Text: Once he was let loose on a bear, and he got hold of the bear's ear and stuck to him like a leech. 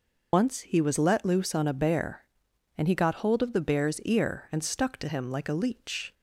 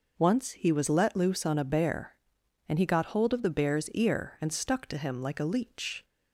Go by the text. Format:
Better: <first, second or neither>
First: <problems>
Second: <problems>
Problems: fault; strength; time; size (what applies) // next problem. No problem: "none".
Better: second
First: loses the start of "Once"; at 0.3 s; 60 ms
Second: none